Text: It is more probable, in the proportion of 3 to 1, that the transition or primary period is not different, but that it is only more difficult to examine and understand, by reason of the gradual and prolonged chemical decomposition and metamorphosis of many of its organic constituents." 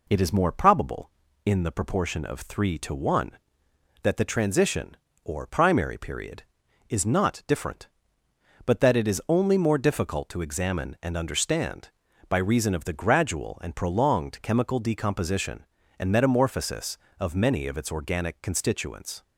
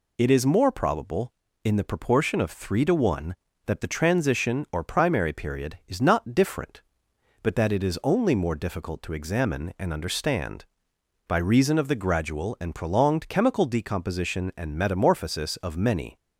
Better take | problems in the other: first | stops before "of its organic constituents"; at 16.1 s

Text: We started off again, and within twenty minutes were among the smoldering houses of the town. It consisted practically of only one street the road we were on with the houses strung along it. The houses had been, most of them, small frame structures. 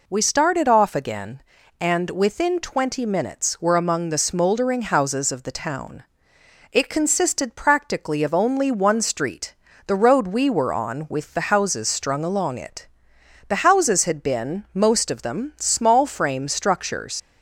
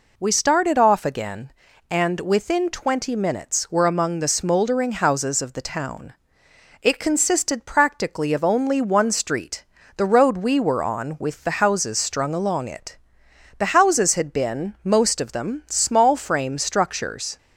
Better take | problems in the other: second | pauses between "street" and "the"; slight; at 9.5 s; 0.32 s long; slight in the second // leaves "structures" unfinished; at 17.1 s; 75 ms

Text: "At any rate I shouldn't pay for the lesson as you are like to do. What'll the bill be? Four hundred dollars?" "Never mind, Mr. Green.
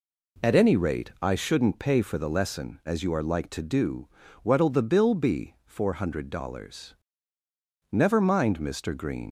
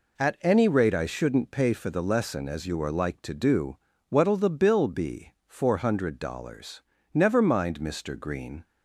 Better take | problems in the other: second | leaves "Green" unfinished; at 9.2 s; 85 ms

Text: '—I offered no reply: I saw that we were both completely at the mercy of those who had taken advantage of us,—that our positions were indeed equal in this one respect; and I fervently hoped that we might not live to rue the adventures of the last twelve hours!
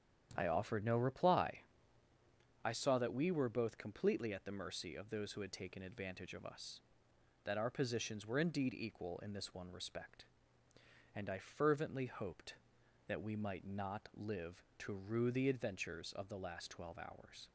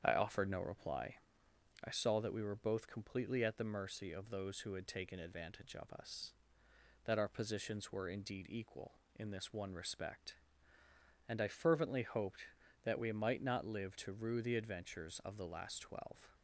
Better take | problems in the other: first | starts louder than the rest; strong; until 1.0 s; 8 dB; strong in the first // stops before "hours"; at 16.3 s

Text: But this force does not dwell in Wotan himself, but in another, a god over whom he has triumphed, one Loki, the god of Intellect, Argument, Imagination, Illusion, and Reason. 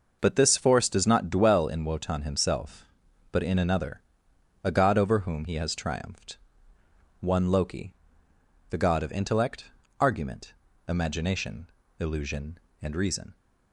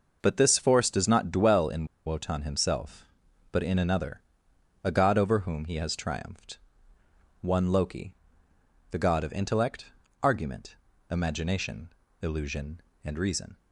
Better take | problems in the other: first | pauses between "in" and "Wotan"; slight; at 1.8 s; 0.19 s long

